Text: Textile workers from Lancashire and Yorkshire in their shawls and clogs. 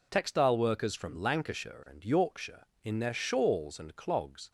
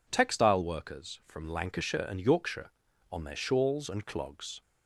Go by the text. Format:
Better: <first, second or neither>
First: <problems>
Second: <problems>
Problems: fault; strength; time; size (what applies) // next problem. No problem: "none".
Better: first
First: none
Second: says "on" for "in"; at 3.1 s